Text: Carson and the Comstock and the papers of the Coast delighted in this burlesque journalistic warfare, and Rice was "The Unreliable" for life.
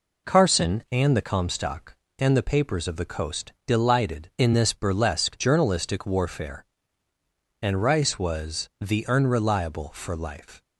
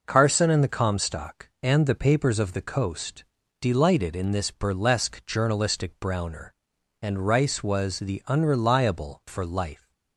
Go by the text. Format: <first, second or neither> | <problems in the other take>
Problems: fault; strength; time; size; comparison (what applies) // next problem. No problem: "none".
first | pauses between "Coast" and "delighted"; at 3.2 s; 0.38 s long // says "browner" for "warfare"; at 5.9 s